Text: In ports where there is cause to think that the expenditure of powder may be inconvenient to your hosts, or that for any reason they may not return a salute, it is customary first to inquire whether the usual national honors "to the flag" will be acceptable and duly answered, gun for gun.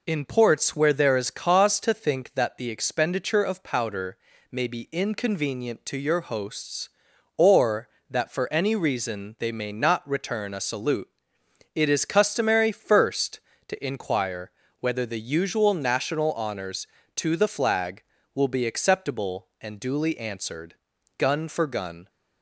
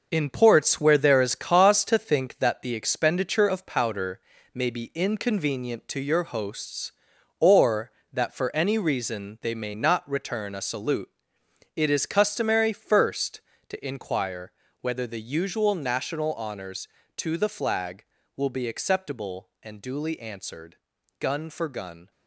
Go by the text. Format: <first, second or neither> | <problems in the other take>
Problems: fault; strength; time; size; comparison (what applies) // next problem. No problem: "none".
first | gets quieter; strong; throughout; 7.5 dB // pauses between "powder" and "may"; slight; at 4.1 s; 0.34 s long; slight in the first // pauses between "inquire" and "whether"; slight; at 14.5 s; 0.30 s long; slight in the first